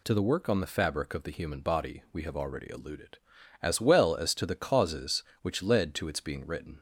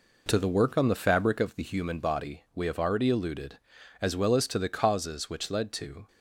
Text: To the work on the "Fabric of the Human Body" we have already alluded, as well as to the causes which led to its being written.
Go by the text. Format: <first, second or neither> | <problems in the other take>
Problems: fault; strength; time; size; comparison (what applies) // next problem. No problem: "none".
first | stops before "its being written"; at 6.0 s